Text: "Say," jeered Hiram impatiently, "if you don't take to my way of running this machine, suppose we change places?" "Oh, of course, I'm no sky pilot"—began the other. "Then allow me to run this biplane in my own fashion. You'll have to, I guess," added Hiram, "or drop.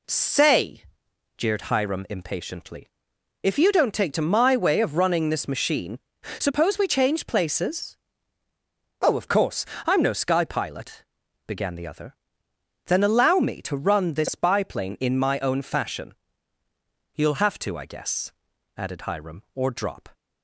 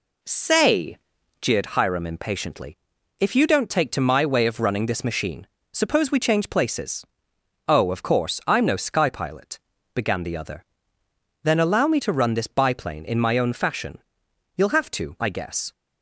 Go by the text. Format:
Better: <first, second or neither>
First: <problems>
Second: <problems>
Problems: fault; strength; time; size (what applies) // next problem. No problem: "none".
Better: first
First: none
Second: stops before "added Hiram or drop"; at 15.7 s